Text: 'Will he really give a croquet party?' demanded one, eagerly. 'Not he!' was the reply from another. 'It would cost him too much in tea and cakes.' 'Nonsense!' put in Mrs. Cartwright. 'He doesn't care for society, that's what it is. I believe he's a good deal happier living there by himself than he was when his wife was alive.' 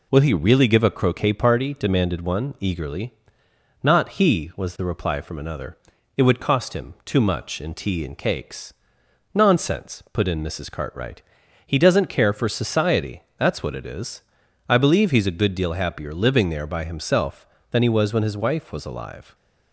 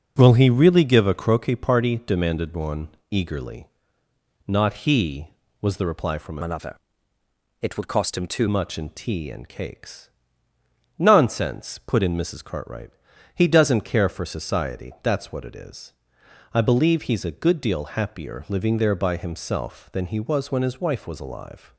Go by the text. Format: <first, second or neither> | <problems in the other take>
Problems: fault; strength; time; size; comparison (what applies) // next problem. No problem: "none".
first | changes voice from "another" to "too"; from 6.4 to 8.4 s; 2.0 s long